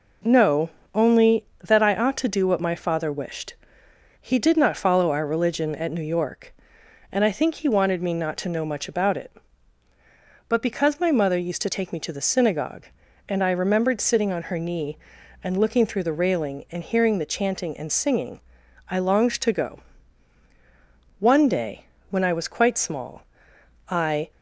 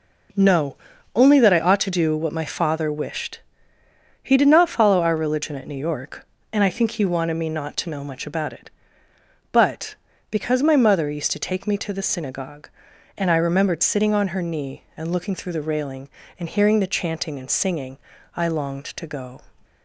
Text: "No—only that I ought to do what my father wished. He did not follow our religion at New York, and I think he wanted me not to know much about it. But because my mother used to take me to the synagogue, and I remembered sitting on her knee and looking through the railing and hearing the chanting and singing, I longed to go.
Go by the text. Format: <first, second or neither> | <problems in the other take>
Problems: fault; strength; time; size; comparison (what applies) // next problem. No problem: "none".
second | goes on to say "One day when I was quite small I"; strong; from 21.1 s on; 3.1 s long